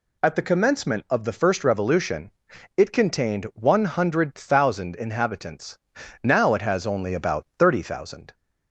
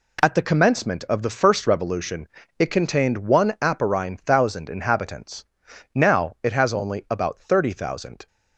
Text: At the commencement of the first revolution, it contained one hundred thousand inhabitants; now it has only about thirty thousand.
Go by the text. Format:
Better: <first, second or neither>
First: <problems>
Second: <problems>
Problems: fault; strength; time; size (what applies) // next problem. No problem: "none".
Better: first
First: none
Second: says "aparine" for "hundred"; at 3.6 s